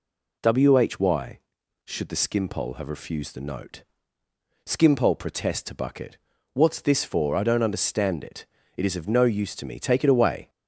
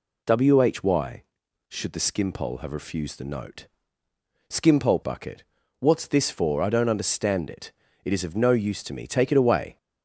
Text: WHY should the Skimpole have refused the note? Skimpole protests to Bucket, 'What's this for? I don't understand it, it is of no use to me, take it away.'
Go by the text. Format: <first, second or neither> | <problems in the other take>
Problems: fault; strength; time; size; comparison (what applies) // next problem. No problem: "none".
first | skips "protests to"; at 5.0 s